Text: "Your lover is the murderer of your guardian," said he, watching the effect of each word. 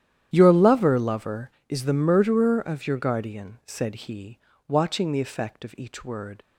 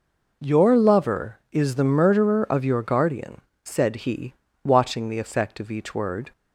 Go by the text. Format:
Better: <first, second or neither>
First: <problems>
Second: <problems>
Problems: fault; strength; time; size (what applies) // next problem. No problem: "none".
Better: second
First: starts louder than the rest; strong; until 1.3 s; 10.5 dB // says "lover" twice; at 0.9 s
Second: none